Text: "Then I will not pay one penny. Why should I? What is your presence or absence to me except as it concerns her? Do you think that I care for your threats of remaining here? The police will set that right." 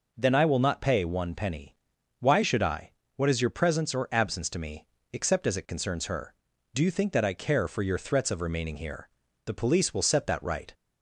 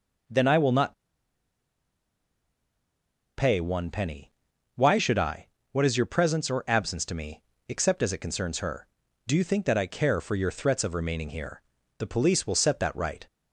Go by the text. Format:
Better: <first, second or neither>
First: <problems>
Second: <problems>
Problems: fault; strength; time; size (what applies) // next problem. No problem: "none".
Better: first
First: pauses between "me" and "except"; slight; at 4.8 s; 0.24 s long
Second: pauses between "not" and "pay"; strong; at 0.9 s; 2.4 s long // pauses between "me" and "except"; slight; at 7.4 s; 0.24 s long